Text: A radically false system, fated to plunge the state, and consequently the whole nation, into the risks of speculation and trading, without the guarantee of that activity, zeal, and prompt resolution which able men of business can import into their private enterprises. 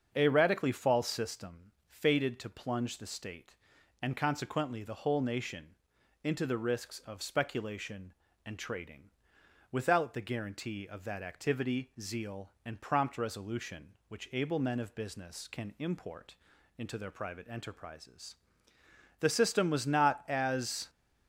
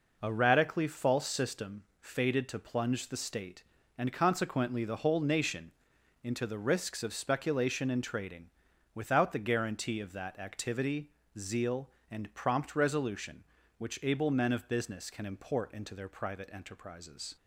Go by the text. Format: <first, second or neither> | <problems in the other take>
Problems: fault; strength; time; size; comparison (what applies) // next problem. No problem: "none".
second | starts louder than the rest; until 1.1 s; 7 dB // pauses between "import" and "into"; at 16.3 s; 0.42 s long // goes on to say "The system was not as"; strong; from 19.1 s on; 1.7 s long